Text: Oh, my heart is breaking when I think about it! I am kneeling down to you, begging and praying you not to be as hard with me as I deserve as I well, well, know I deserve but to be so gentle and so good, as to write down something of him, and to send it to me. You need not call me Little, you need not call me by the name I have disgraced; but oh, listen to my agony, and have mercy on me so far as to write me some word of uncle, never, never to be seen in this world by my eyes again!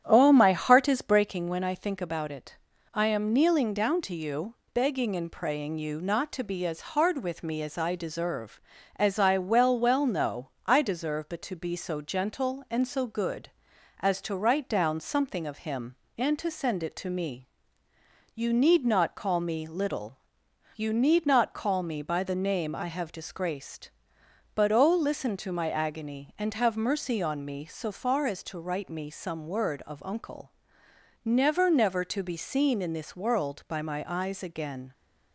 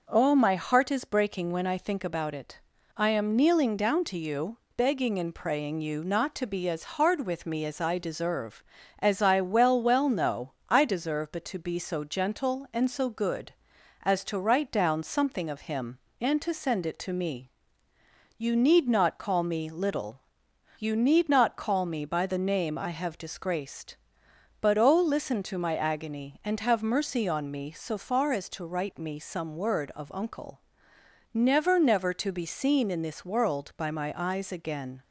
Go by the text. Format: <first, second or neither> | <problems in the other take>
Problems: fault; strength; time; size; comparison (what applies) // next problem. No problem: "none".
second | starts louder than the rest; strong; until 1.4 s; 10 dB // pauses between "know" and "I"; slight; at 10.4 s; 0.16 s long; slight in the second